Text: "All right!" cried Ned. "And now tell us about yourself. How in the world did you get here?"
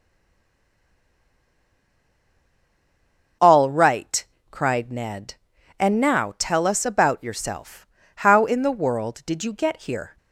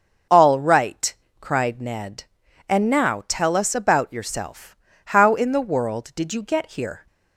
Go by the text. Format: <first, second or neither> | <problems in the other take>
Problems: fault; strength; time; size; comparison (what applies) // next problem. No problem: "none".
second | stays silent before the first word; strong; until 3.4 s; 3.4 s long // starts louder than the rest; until 4.6 s; 6.5 dB; also in the second